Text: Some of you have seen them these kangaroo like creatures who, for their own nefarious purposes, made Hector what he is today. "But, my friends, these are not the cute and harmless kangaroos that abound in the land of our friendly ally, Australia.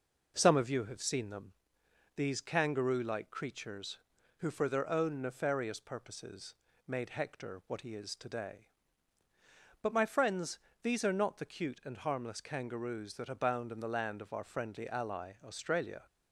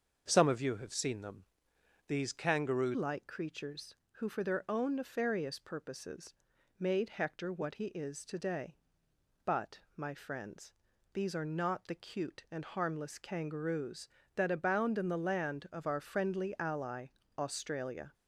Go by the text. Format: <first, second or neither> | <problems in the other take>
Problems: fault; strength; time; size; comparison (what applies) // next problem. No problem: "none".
first | starts louder than the rest; until 1.3 s; 6.5 dB // pauses between "them" and "these"; noticeable; at 1.4 s; 0.64 s long; noticeable in the first // changes voice at "like"; from 2.9 s on; 15.2 s long